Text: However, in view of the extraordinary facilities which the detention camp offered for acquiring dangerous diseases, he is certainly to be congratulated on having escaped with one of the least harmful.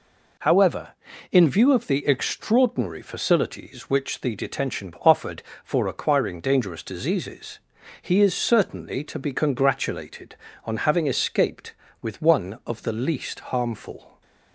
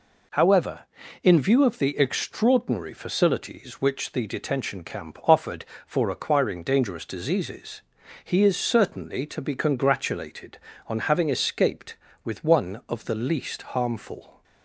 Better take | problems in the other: second | skips "camp"; at 4.9 s

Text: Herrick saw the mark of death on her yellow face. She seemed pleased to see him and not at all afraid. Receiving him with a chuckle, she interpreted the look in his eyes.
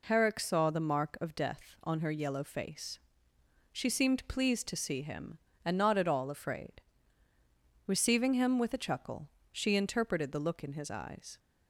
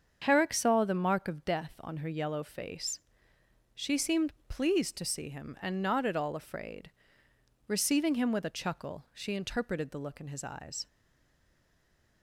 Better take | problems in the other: first | starts louder than the rest; strong; until 1.2 s; 7 dB // pauses between "seemed" and "pleased"; slight; at 4.3 s; 0.16 s long // stays silent after the last word; noticeable; from 10.8 s on; 1.4 s long

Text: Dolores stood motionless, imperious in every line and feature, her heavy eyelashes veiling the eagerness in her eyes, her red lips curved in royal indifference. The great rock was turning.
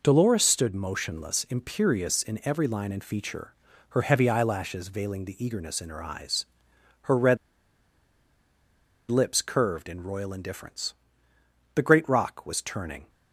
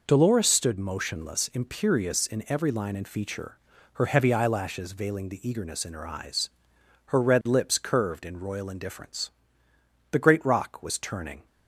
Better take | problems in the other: second | pauses between "red" and "lips"; strong; at 7.3 s; 1.7 s long

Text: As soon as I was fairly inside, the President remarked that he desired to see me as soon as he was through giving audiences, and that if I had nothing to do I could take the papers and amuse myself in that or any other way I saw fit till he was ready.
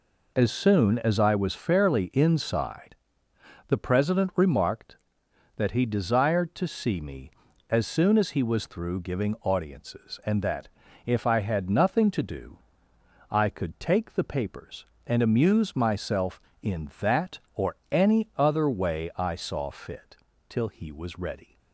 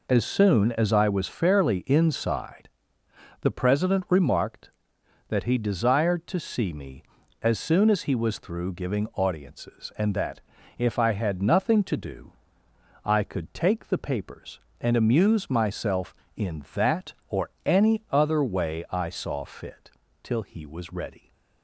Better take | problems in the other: neither | pauses between "that" and "if"; the same in both // pauses between "do" and "I"; noticeable; the same in both // pauses between "fit" and "till"; slight; the same in both

